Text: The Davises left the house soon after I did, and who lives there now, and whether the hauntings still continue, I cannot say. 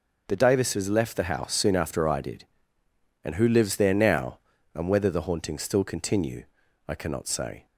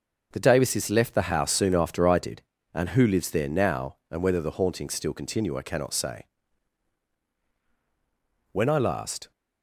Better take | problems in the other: first | starts louder than the rest; noticeable; until 1.3 s; 6 dB // goes on to say "When I last"; noticeable; from 8.5 s on; 0.78 s long

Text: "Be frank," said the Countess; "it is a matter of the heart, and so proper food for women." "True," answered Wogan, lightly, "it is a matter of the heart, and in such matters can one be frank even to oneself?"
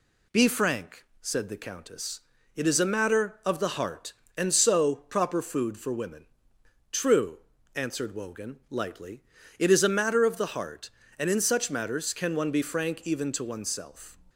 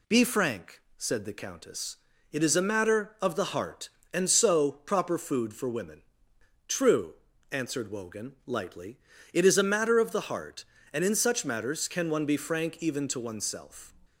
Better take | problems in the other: neither | none

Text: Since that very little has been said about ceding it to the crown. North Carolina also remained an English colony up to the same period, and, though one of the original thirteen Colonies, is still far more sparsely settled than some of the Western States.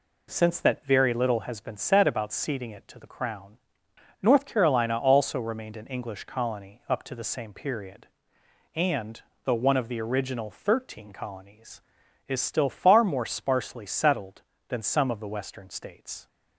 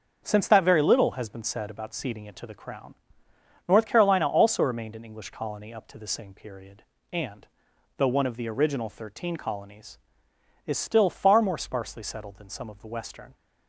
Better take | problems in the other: first | starts louder than the rest; until 1.2 s; 7 dB // stops before "States"; at 13.3 s

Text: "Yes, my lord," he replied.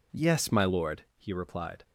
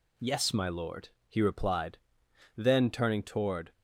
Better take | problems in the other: first | goes on to say "Then turning toward"; noticeable; from 2.5 s on; 1.1 s long

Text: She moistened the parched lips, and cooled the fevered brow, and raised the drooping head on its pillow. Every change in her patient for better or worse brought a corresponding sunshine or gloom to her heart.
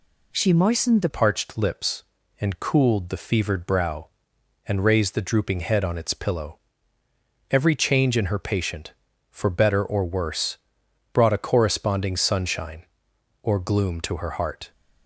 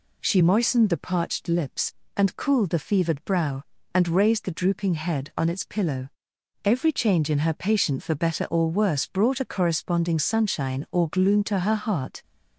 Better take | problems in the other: second | changes voice at "parched"; from 1.0 s on; 13.7 s long // pauses between "worse" and "brought"; noticeable; at 10.5 s; 0.56 s long

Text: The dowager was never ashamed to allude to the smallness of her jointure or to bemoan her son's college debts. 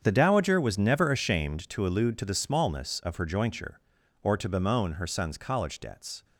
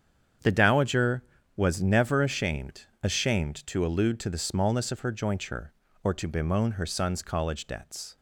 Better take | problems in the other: first | starts louder than the rest; strong; until 1.7 s; 8 dB; strong in the first // says "ashamed" twice; at 3.0 s

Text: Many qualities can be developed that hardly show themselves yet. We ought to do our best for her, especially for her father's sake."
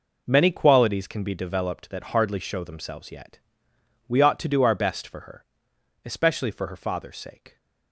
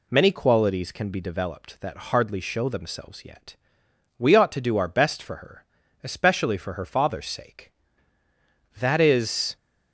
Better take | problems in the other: first | goes on to say "That is"; noticeable; from 8.7 s on; 0.78 s long

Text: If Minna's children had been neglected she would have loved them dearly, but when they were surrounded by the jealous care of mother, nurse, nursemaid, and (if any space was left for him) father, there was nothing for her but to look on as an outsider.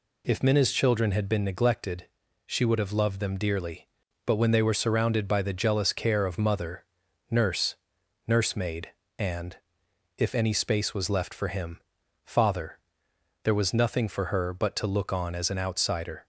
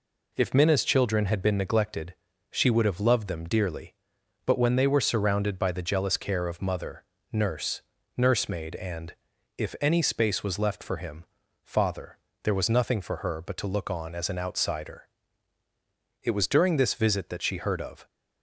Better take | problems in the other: first | pauses between "neglected" and "she"; at 2.1 s; 0.40 s long; also in the first // goes on to say "It was during this visit that she heard of"; strong; from 16.2 s on; 1.8 s long

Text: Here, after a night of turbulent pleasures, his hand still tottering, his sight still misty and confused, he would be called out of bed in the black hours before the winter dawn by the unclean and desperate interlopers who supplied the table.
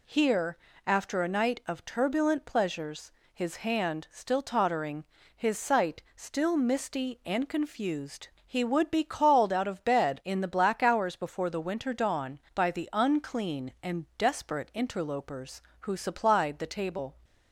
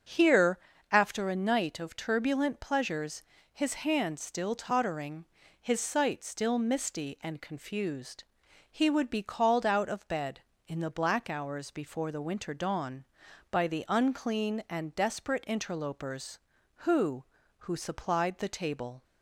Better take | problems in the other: first | starts louder than the rest; until 1.4 s; 7 dB // says "who" twice; at 17.5 s

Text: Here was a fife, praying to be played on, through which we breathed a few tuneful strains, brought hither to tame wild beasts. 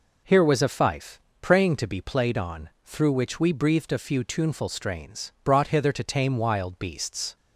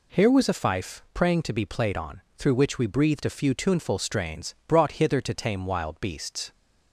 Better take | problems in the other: neither | none

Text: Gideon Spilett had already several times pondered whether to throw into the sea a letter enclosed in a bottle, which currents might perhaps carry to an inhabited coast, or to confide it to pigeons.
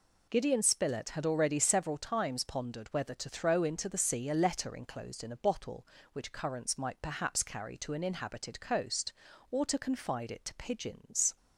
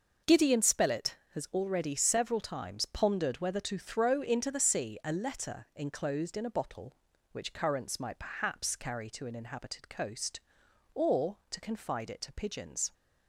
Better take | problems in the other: first | starts louder than the rest; noticeable; until 1.3 s; 6 dB // says "has" for "had"; at 1.3 s

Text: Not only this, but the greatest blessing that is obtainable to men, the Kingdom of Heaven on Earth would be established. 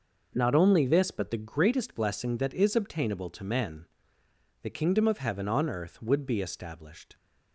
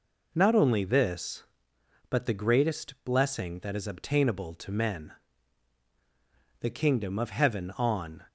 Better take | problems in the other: first | stops before "Earth would be established"; at 8.2 s

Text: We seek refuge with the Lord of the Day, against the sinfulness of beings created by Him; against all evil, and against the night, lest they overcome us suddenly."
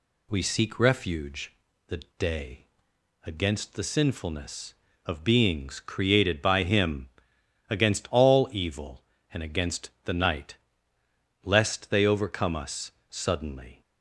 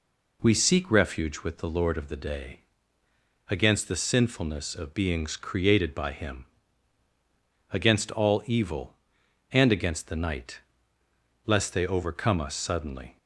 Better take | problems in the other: second | skips "with the Lord of"; at 1.7 s // pauses between "the" and "Day"; slight; at 1.9 s; 0.19 s long // pauses between "us" and "suddenly"; slight; at 12.9 s; 0.18 s long

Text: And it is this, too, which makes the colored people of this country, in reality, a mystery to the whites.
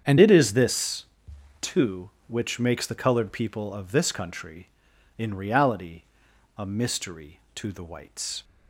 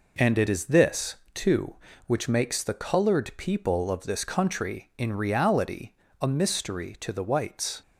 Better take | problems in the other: second | starts louder than the rest; strong; until 1.6 s; 8 dB // changes voice at "it"; from 0.1 s on; 8.3 s long

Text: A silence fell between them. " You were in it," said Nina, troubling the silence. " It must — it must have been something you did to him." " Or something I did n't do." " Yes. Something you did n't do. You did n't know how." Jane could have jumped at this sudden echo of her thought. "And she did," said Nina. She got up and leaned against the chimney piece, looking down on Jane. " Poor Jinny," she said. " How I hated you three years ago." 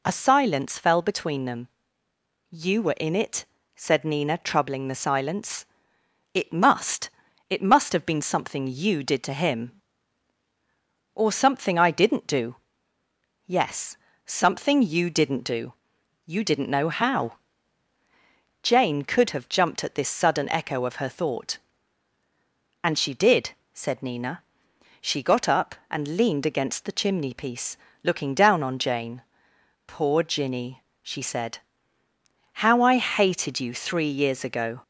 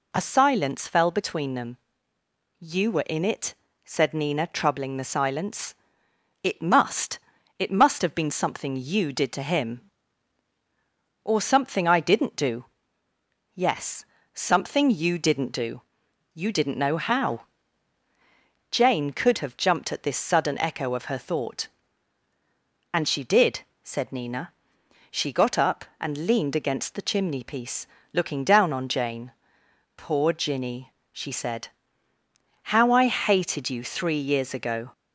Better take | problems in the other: neither | none

